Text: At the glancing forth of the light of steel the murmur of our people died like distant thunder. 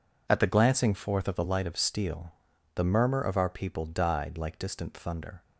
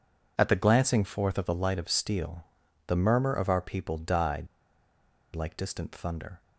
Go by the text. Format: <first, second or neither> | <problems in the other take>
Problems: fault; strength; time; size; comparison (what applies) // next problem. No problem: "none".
first | pauses between "steel" and "the"; at 2.4 s; 0.44 s long; also in the first // pauses between "died" and "like"; noticeable; at 4.4 s; 0.86 s long